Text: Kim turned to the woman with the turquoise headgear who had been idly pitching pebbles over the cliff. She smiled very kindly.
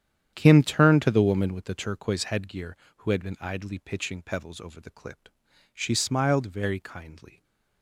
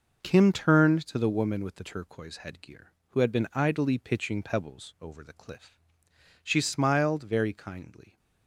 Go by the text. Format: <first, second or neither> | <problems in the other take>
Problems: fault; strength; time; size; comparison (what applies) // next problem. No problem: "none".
second | starts louder than the rest; strong; until 1.3 s; 9.5 dB // says "clip" for "cliff"; at 4.9 s // stays silent after the last word; slight; from 7.2 s on; 0.6 s long